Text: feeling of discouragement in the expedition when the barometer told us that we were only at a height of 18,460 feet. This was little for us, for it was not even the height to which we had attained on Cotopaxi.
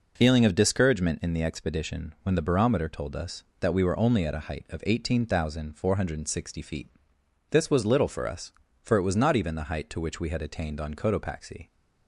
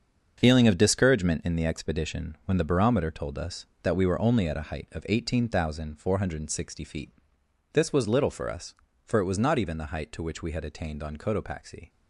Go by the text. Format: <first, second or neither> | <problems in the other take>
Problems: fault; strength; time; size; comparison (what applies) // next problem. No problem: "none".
first | gets quieter; strong; throughout; 8.5 dB